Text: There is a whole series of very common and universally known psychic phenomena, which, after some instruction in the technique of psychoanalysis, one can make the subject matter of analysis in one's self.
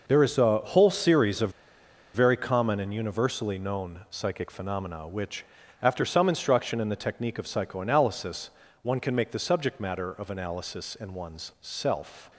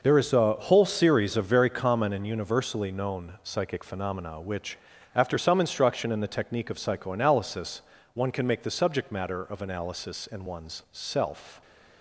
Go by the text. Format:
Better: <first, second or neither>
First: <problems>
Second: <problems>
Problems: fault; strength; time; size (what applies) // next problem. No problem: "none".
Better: second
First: pauses between "of" and "very"; noticeable; at 1.5 s; 0.63 s long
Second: none